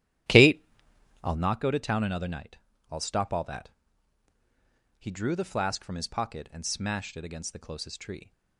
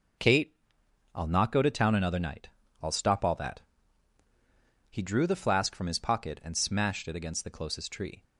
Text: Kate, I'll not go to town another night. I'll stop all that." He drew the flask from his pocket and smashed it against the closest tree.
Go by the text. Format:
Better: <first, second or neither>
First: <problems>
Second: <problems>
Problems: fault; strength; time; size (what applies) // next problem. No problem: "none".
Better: second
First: starts louder than the rest; strong; until 1.5 s; 12.5 dB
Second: none